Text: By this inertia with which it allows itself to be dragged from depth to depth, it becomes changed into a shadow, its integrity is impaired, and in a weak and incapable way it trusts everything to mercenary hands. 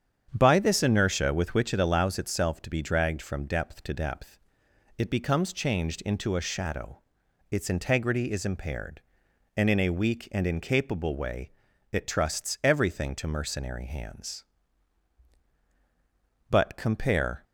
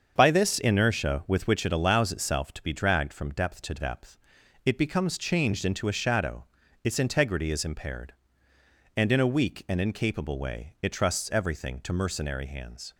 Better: second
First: starts louder than the rest; strong; until 1.3 s; 8.5 dB // pauses between "way" and "it"; at 11.4 s; 0.42 s long // goes on to say "But compare"; noticeable; from 16.5 s on; 0.92 s long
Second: starts louder than the rest; until 1.1 s; 7 dB

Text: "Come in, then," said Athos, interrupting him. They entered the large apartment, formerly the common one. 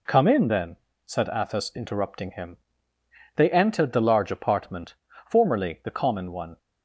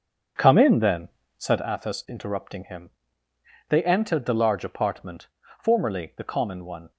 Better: first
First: none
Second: starts louder than the rest; strong; until 1.7 s; 7.5 dB

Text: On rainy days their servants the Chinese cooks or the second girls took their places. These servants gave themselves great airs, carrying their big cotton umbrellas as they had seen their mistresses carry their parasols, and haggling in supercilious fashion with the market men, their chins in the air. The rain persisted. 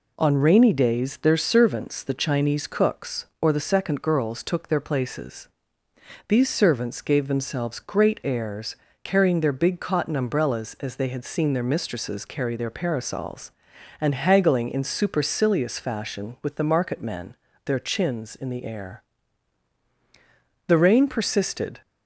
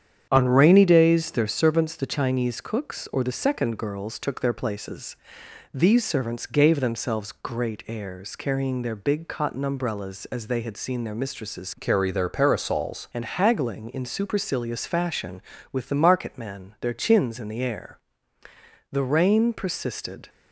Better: first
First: none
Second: starts louder than the rest; strong; until 1.3 s; 9 dB // changes voice from "carry" to "parasols"; from 11.7 to 13.0 s; 1.3 s long

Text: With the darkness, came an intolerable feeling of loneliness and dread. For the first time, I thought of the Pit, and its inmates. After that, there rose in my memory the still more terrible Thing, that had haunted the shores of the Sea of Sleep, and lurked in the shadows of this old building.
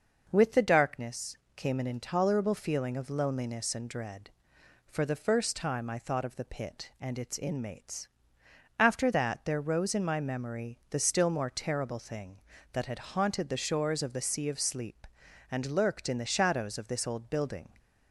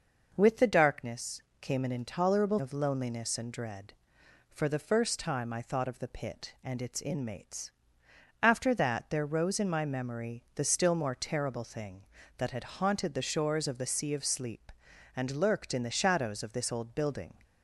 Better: first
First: none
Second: skips "feeling"; at 2.5 s

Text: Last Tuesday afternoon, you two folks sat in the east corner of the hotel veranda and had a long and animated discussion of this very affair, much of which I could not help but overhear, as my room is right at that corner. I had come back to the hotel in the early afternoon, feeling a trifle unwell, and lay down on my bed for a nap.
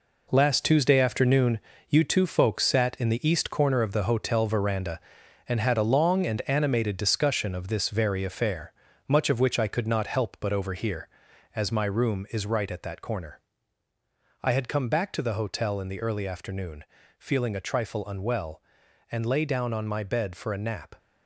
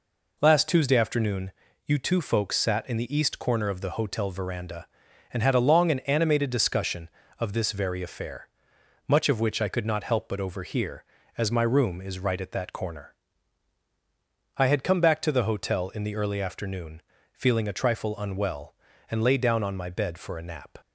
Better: second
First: gets quieter; strong; throughout; 8 dB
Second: none

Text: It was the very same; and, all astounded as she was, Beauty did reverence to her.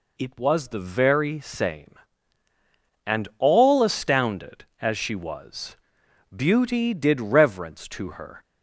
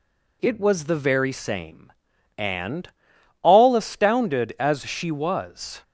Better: first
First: none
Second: stops before "Beauty did reverence to her"; at 5.8 s

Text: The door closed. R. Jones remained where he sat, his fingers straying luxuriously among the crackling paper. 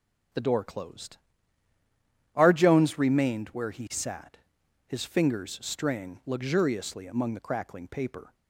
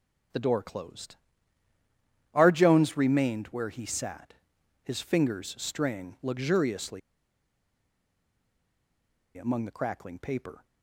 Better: first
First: starts louder than the rest; strong; until 2.5 s; 7.5 dB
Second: starts louder than the rest; strong; until 2.4 s; 7.5 dB // pauses between "luxuriously" and "among"; strong; at 7.0 s; 2.3 s long

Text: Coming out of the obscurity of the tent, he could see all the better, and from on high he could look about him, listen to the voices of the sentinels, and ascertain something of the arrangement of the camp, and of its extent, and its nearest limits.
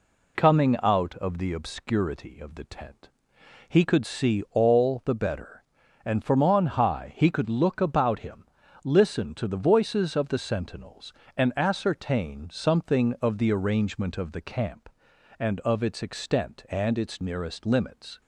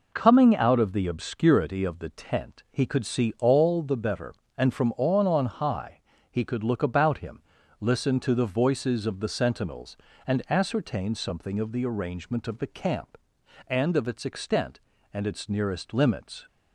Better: first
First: none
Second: says "on" twice; at 5.2 s // pauses between "high" and "he"; slight; at 6.0 s; 0.28 s long

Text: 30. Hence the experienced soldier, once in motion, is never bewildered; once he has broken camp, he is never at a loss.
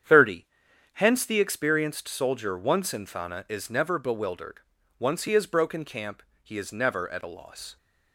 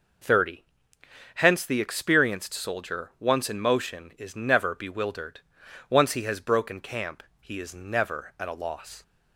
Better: second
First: starts louder than the rest; strong; until 1.5 s; 8.5 dB // says "thana" for "motion"; at 3.0 s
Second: none

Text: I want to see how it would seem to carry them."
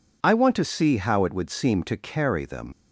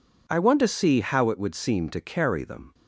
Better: second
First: leaves "them" unfinished; at 2.7 s; 100 ms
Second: none

